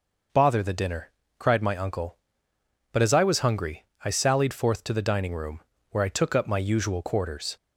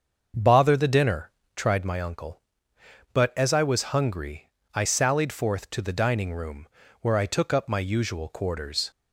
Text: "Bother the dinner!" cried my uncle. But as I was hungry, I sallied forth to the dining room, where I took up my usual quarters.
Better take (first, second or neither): first